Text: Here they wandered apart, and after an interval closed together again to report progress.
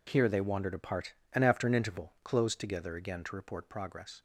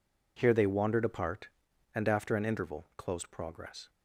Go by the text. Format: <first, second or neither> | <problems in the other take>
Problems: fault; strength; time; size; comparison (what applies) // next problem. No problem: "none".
first | skips "together again to report"; at 3.3 s